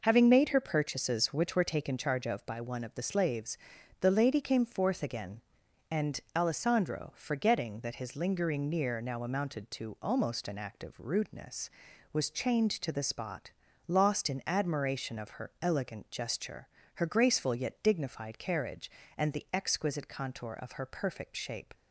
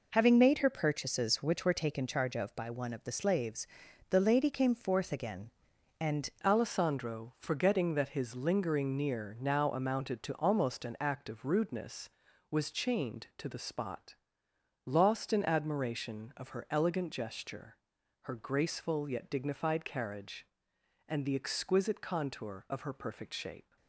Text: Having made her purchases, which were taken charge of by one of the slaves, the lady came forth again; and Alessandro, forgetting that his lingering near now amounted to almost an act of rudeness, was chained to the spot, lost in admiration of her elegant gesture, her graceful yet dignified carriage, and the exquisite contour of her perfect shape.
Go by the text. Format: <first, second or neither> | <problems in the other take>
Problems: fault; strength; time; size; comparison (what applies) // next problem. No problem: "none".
first | changes voice at "Alessandro"; from 6.4 s on; 17.3 s long